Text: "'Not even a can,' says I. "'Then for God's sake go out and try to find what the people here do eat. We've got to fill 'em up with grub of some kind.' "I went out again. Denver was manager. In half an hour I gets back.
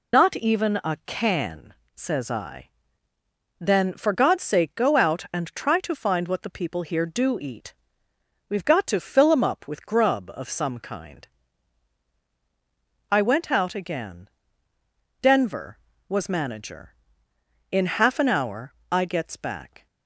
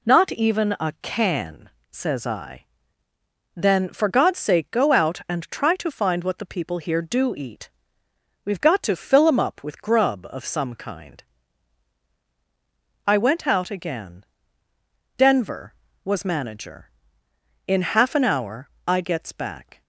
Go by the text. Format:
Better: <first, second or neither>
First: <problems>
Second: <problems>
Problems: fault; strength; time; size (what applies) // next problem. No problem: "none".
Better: second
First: loses the start of "Not"; at 0.1 s; 55 ms // pauses between "hour" and "I"; slight; at 18.7 s; 0.18 s long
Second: pauses between "hour" and "I"; slight; at 18.6 s; 0.18 s long